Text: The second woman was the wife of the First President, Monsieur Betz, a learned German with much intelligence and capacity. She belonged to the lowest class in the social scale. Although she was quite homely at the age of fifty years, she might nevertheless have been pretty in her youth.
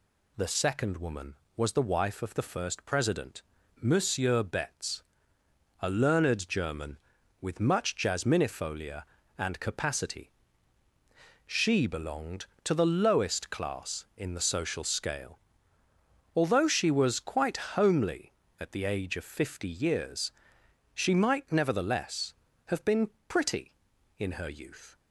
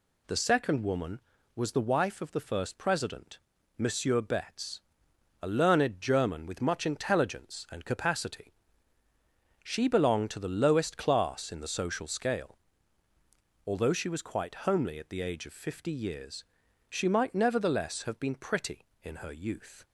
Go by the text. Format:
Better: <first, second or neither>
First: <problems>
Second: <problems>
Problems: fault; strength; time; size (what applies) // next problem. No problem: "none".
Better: second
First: says "jasminifolia" for "intelligence"; at 7.9 s // pauses between "been" and "pretty"; slight; at 23.1 s; 0.18 s long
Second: none